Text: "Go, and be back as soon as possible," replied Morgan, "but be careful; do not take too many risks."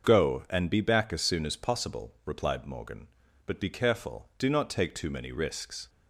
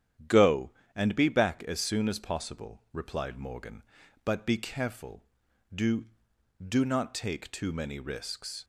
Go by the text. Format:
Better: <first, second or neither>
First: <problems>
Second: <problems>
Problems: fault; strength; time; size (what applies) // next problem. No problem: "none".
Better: first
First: starts louder than the rest; until 1.1 s; 6.5 dB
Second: starts louder than the rest; strong; until 1.5 s; 9.5 dB // says "do" twice; at 6.6 s